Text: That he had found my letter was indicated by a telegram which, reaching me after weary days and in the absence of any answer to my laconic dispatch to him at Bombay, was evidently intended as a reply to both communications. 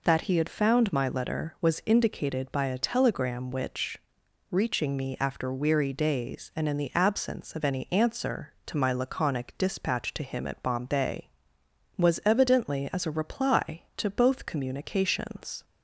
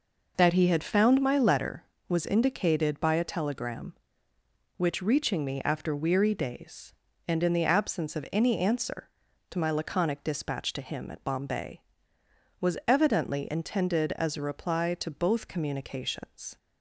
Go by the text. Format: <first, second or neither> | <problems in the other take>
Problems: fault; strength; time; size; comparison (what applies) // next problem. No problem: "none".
second | skips "intended"; at 12.9 s